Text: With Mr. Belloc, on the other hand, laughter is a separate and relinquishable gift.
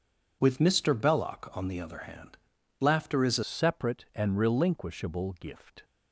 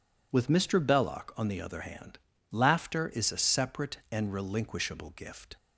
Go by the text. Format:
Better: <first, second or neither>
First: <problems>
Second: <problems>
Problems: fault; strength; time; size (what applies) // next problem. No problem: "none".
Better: second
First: changes voice at "separate"; from 3.4 s on; 2.4 s long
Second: none